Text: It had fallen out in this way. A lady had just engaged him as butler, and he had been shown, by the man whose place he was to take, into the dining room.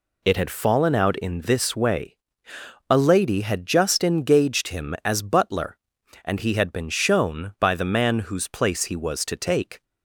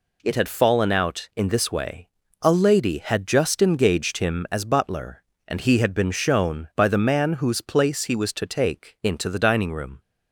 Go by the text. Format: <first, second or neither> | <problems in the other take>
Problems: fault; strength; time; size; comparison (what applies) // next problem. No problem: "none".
second | stops before "into the dining room"; at 9.8 s